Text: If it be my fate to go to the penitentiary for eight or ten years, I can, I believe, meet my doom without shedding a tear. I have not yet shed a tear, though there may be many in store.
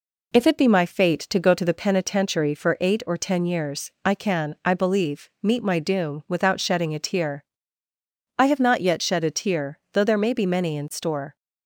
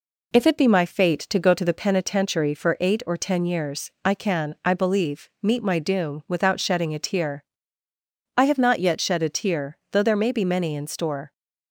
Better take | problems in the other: neither | none

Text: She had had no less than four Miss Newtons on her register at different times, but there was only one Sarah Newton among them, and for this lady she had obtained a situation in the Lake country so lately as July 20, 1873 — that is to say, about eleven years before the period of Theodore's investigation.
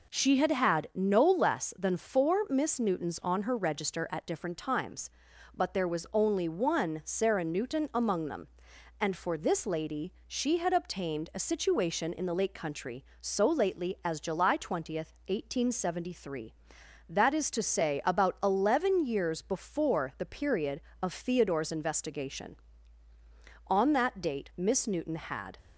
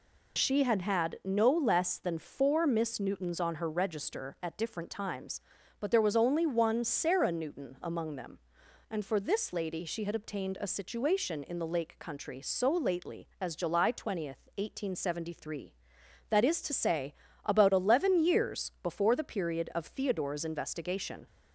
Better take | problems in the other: second | pauses between "lady" and "she"; slight; at 10.1 s; 0.16 s long // goes on to say "On that date Miss Newton had"; strong; from 23.6 s on; 1.9 s long

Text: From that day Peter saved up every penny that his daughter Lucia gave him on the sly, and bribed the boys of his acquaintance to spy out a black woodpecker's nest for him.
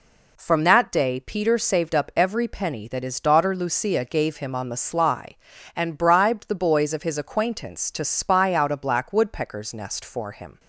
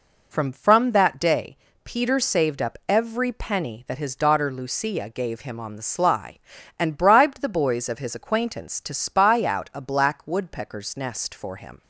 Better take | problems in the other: first | says "From" twice; at 0.5 s // pauses between "day" and "Peter"; slight; at 1.5 s; 0.26 s long

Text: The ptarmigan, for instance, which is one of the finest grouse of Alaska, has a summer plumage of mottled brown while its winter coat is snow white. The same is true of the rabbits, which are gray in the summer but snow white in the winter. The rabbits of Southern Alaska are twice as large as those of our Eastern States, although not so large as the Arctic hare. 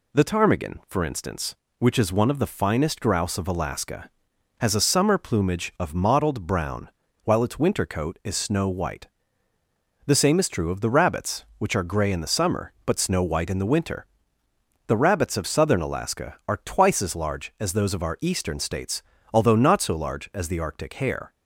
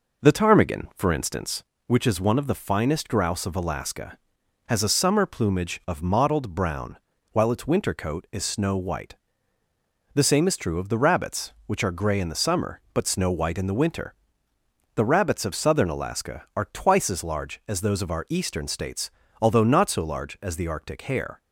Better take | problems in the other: first | starts louder than the rest; noticeable; until 1.6 s; 5 dB // pauses between "brown" and "while"; slight; at 6.9 s; 0.36 s long; slight in the first

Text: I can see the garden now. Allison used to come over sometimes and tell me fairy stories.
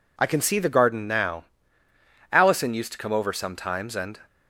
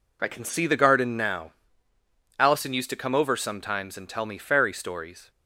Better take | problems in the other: second | stops before "tell me fairy stories"; at 4.2 s

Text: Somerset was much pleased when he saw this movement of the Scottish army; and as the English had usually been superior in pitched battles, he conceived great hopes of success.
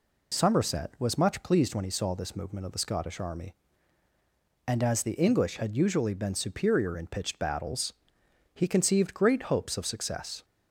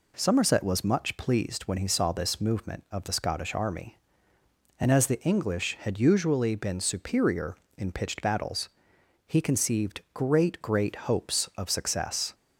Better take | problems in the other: first | says "great" twice; at 10.6 s

